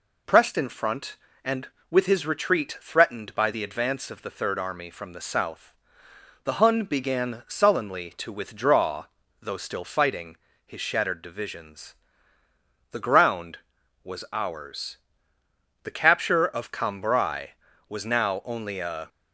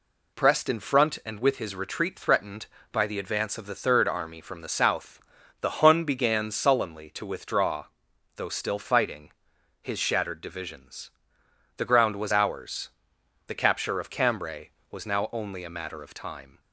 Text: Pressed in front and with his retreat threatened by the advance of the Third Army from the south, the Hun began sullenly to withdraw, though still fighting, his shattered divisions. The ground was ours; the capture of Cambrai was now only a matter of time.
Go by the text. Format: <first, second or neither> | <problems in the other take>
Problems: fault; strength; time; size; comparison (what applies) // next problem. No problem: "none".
second | stops before "matter of time"; at 19.0 s